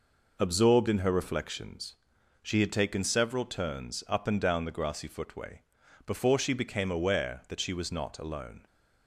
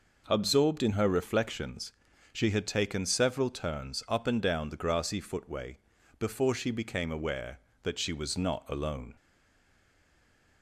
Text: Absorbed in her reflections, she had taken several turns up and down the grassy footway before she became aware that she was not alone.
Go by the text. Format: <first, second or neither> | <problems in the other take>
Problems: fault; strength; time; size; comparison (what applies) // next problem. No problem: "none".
first | pauses between "footway" and "before"; at 5.7 s; 0.40 s long; also in the first // stays silent after the last word; noticeable; from 9.1 s on; 1.5 s long